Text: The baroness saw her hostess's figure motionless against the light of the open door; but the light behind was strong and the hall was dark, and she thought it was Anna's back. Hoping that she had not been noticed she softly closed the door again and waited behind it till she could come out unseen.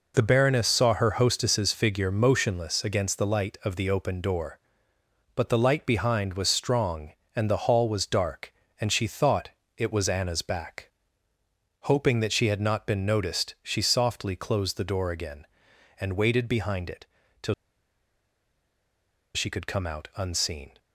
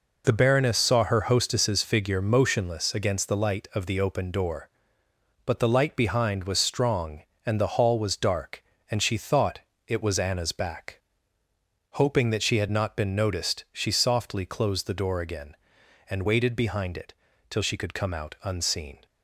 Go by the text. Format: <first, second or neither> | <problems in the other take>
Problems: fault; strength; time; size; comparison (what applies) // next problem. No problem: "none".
second | pauses between "thought" and "it"; slight; at 9.4 s; 0.26 s long; slight in the second // pauses between "it" and "till"; slight; at 17.0 s; 0.36 s long; slight in the second // pauses between "till" and "she"; strong; at 17.5 s; 1.8 s long